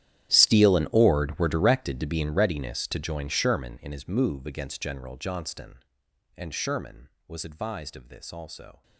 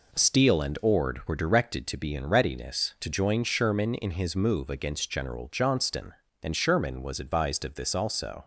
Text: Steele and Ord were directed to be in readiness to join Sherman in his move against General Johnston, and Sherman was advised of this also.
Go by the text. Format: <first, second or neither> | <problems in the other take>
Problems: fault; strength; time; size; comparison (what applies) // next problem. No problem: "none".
second | gets quieter; strong; throughout; 19.5 dB